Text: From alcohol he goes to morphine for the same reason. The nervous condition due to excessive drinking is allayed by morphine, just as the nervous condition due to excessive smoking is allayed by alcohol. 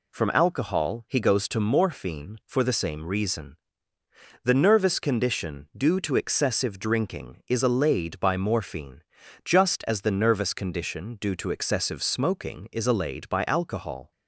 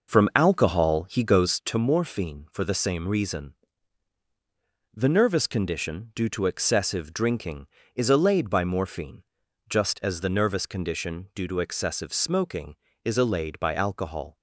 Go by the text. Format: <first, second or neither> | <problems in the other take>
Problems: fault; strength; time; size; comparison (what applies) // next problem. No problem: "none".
first | starts louder than the rest; noticeable; until 1.8 s; 5.5 dB